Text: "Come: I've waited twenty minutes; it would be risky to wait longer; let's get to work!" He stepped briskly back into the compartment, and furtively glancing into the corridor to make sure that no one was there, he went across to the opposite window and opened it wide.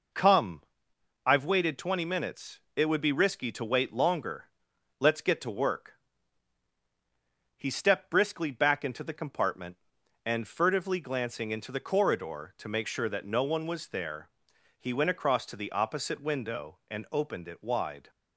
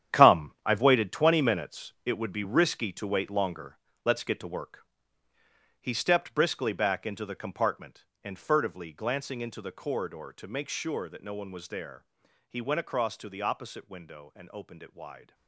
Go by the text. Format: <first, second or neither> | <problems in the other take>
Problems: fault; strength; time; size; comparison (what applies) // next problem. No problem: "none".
first | gets quieter; strong; throughout; 12 dB